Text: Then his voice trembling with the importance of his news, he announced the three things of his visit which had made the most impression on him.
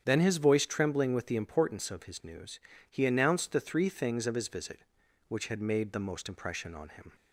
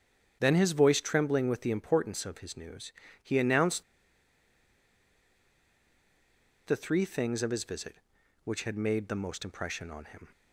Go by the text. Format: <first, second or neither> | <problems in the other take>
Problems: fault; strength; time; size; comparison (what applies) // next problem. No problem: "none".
first | starts louder than the rest; strong; until 1.4 s; 8.5 dB; strong in the first // pauses between "announced" and "the"; strong; at 3.8 s; 2.8 s long